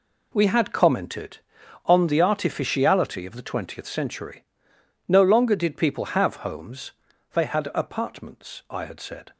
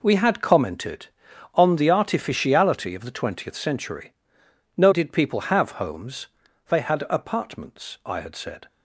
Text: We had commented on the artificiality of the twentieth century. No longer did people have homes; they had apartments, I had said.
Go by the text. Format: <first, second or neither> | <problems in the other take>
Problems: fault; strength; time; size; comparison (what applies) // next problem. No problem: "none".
first | skips "longer"; at 4.9 s